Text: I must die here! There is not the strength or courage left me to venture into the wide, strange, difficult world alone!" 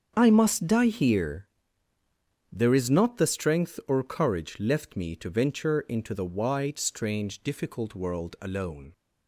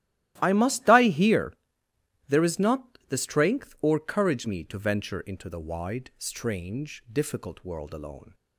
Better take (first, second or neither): first